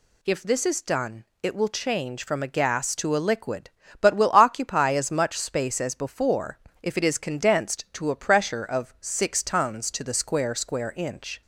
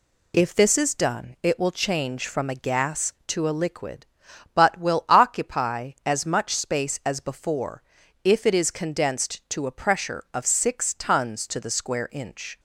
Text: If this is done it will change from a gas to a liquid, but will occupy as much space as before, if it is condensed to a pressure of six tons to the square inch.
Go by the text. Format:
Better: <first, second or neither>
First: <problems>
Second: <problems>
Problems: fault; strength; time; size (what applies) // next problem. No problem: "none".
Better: second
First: pauses between "done" and "it"; slight; at 1.2 s; 0.18 s long // says "square" twice; at 10.5 s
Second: none